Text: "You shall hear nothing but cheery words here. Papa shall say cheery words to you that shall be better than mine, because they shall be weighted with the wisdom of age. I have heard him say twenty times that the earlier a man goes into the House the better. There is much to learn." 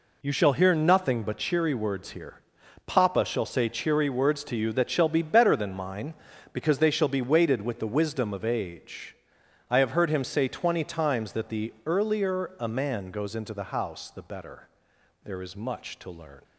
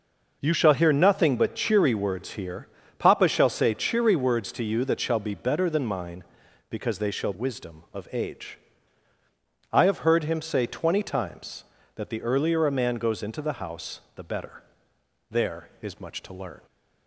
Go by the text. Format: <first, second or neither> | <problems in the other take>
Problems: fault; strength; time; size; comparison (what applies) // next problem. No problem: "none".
first | skips "be weighted with the"; at 7.3 s // pauses between "House" and "the"; slight; at 13.9 s; 0.16 s long